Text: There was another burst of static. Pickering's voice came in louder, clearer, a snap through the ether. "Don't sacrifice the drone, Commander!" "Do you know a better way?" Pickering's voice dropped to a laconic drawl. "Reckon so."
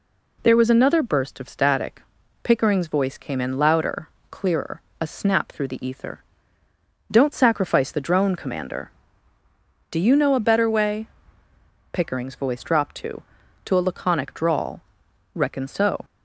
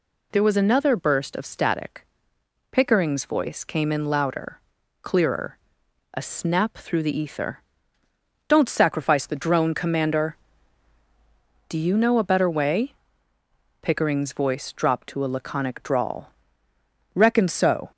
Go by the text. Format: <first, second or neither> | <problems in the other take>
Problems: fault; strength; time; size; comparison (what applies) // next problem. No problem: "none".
second | says "to" twice; at 13.6 s